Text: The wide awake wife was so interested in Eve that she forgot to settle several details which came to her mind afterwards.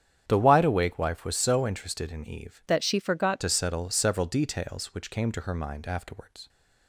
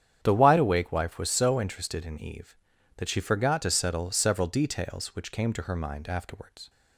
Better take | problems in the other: second | starts louder than the rest; strong; until 1.2 s; 9 dB; strong in the second // changes voice from "that" to "forgot"; from 2.6 to 3.4 s; 0.8 s long

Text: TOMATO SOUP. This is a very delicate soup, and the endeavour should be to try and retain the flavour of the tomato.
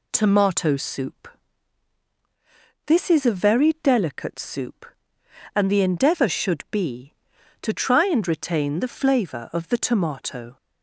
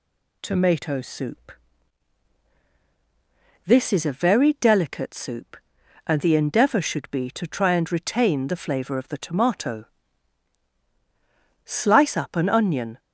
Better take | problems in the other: first | goes on to say "Slice up an onion"; from 11.6 s on; 1.3 s long

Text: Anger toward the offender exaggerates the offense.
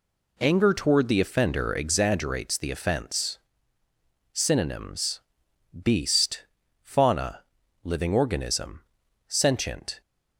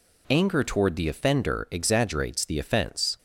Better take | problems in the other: second | goes on to say "Synonyms beast fauna living organism sentient"; strong; from 4.3 s on; 5.6 s long

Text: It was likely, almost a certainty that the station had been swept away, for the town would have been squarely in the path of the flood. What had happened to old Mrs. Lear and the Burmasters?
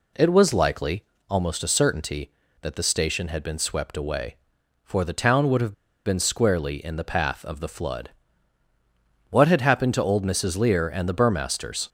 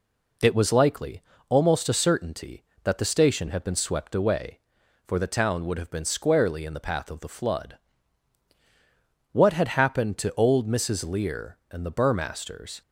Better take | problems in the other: second | pauses between "have" and "been"; slight; at 5.7 s; 0.32 s long

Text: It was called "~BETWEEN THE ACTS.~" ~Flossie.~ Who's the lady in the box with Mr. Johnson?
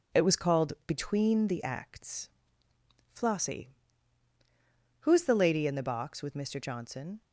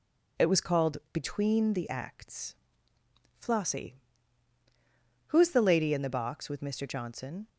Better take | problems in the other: second | gets quieter; noticeable; throughout; 5.5 dB

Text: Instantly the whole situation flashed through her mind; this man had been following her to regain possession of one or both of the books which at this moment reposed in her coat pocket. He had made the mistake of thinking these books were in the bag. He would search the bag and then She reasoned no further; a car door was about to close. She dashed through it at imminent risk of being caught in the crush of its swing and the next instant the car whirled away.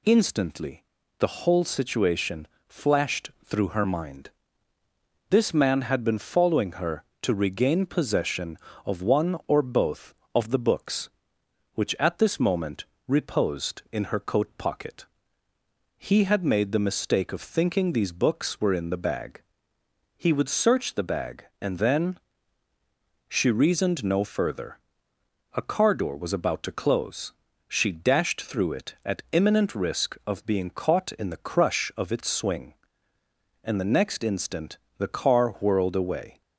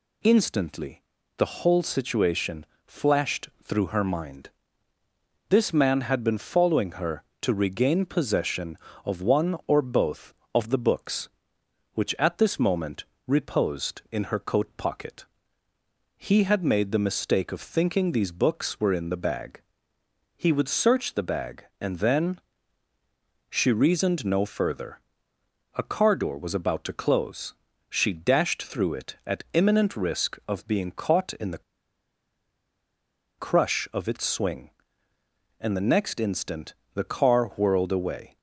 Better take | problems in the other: first | pauses between "Instantly" and "the"; slight; at 1.0 s; 0.34 s long; slight in the first // pauses between "situation" and "flashed"; slight; at 2.6 s; 0.20 s long; slight in the first // pauses between "moment" and "reposed"; slight; at 13.0 s; 0.22 s long; slight in the first // pauses between "then" and "She"; at 22.3 s; 1.1 s long; also in the first // pauses between "the" and "crush"; strong; at 31.6 s; 1.7 s long // pauses between "instant" and "the"; slight; at 36.7 s; 0.20 s long; slight in the first

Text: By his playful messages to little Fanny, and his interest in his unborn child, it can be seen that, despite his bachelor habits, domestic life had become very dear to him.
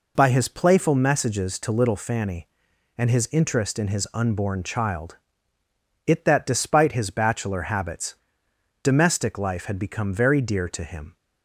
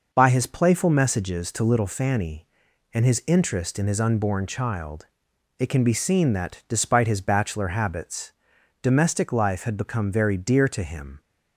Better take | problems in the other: second | skips "can be seen"; at 6.2 s

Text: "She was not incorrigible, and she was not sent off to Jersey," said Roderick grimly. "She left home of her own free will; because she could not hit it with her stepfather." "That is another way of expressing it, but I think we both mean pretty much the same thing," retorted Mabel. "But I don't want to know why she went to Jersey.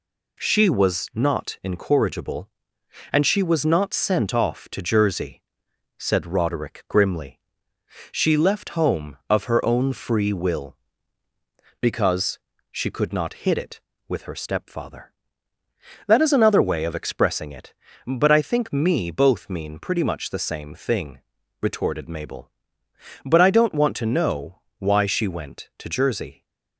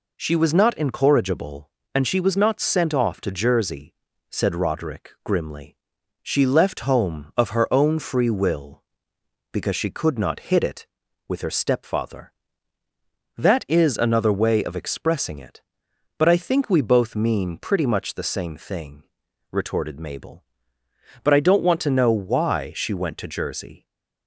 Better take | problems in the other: second | pauses between "because" and "she"; slight; at 12.3 s; 0.32 s long // says "me" for "we"; at 18.7 s // pauses between "know" and "why"; slight; at 24.6 s; 0.20 s long

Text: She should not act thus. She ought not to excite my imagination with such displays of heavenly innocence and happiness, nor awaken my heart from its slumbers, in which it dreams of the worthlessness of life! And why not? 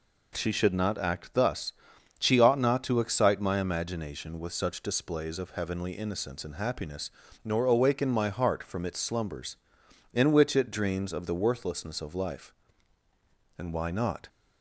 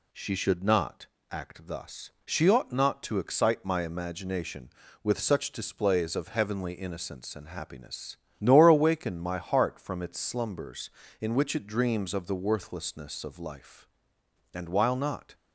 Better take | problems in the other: first | pauses between "not" and "act"; slight; at 1.0 s; 0.24 s long // says "while" for "why"; at 14.6 s

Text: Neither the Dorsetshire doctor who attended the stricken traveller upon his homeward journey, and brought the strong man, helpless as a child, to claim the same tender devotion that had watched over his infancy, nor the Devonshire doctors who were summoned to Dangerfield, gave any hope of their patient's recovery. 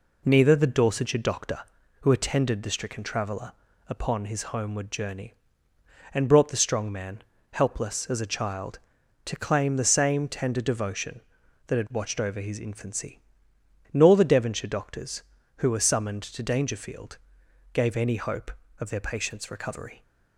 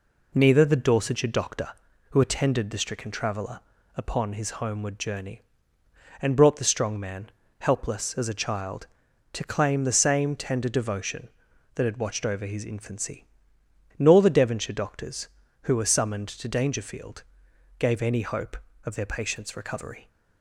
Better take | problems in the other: neither | pauses between "traveller" and "upon"; slight; the same in both

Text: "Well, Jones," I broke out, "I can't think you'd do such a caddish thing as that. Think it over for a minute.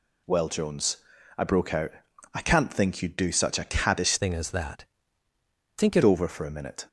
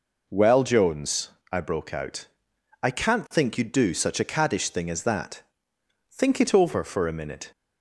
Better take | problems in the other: second | changes voice from "thing" to "it"; from 4.1 to 6.0 s; 1.9 s long

